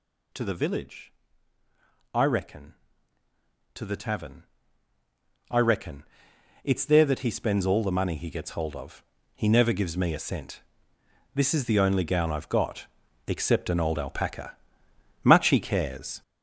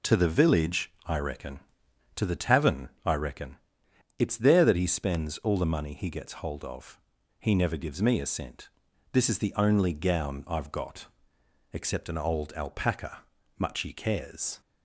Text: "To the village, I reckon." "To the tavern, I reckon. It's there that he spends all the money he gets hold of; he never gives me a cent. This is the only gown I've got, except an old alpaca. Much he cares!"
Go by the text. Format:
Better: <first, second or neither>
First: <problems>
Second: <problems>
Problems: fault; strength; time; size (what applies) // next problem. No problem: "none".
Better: second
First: gets louder; throughout; 6.5 dB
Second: none